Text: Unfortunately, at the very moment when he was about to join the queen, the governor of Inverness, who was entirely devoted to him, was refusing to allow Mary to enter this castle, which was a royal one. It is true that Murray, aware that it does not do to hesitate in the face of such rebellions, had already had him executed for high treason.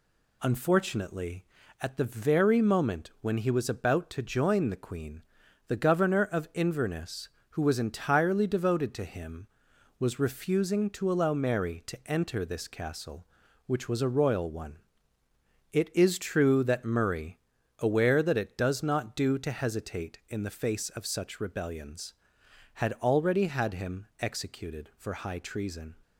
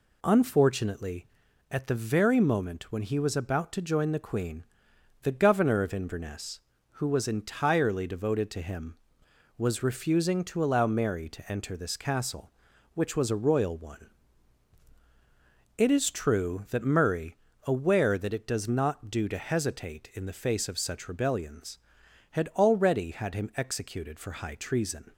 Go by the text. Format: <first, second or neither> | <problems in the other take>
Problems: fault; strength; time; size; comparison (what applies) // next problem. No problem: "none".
neither | none